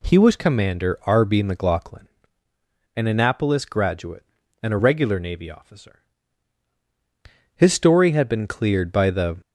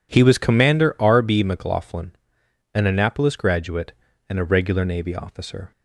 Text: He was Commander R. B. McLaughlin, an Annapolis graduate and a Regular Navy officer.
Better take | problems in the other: second | goes on to say "His story had been cleared by the"; strong; from 7.5 s on; 1.8 s long

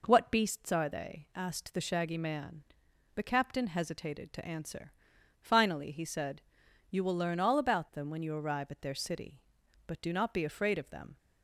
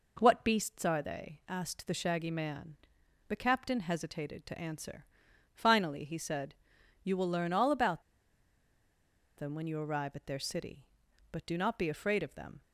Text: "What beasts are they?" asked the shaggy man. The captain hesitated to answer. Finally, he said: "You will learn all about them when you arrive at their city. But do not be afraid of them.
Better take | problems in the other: first | pauses between "about" and "them"; strong; at 8.0 s; 1.3 s long

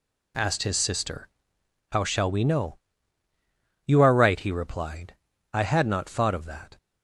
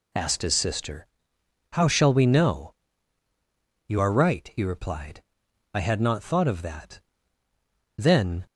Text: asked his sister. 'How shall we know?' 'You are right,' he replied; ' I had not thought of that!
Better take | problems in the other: first | goes on to say "Then"; slight; from 7.9 s on; 0.48 s long

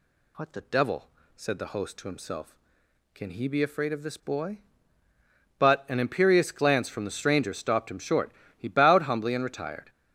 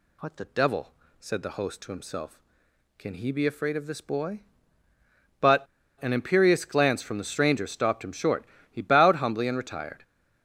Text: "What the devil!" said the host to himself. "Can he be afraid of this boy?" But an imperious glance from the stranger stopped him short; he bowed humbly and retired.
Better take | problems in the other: first | pauses between "But" and "an"; slight; at 5.6 s; 0.35 s long

